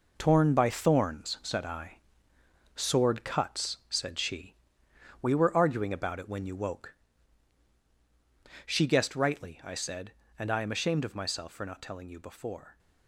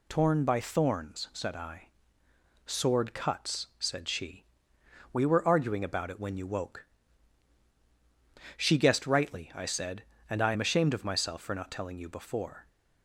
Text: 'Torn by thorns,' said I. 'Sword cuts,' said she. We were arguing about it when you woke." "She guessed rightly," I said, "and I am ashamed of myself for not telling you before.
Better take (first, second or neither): second